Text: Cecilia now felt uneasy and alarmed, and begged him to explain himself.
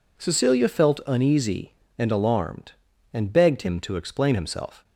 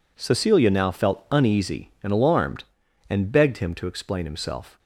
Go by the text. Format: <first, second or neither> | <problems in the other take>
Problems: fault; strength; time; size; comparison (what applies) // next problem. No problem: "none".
second | skips "now"; at 0.6 s